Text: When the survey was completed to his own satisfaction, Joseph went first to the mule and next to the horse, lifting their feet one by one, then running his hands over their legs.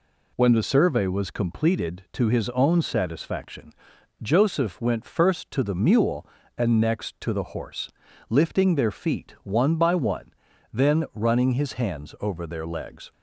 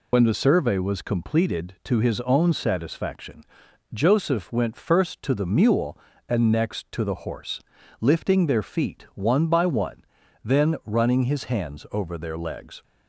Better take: first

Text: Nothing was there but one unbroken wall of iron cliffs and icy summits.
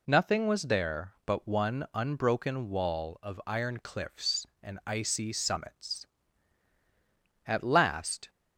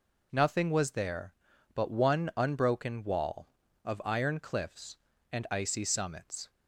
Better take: second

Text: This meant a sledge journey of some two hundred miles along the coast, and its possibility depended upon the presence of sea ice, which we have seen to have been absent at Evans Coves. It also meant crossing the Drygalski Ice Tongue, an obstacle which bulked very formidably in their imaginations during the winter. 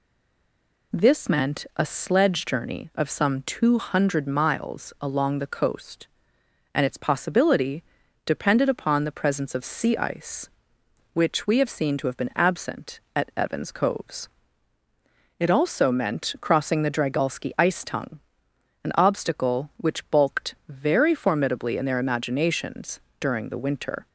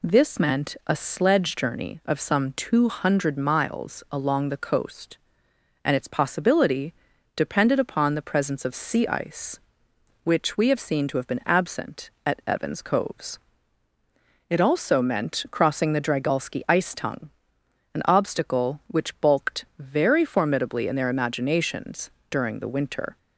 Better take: second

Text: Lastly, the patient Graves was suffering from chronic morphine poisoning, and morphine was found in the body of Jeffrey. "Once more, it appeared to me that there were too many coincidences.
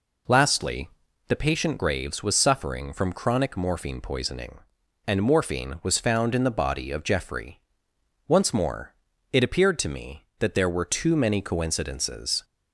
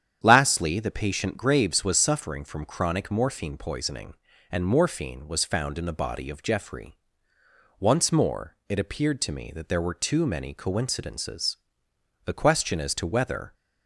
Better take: first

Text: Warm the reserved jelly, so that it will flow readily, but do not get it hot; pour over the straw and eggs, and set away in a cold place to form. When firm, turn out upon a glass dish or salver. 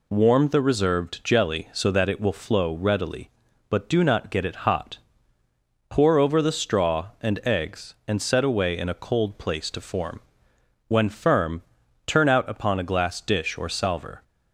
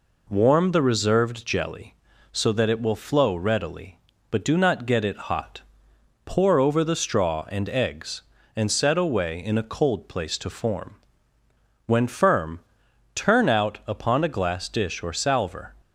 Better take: neither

